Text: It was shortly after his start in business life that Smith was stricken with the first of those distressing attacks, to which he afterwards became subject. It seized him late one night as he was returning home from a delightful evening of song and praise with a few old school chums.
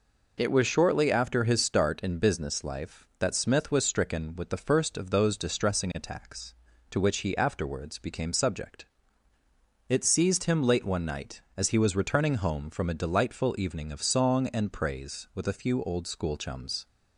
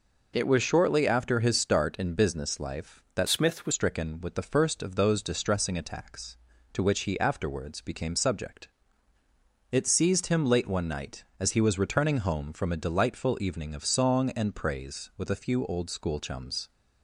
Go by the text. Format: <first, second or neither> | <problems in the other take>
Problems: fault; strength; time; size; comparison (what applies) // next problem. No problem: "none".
first | changes voice from "Smith" to "was"; from 3.2 to 3.7 s; 0.5 s long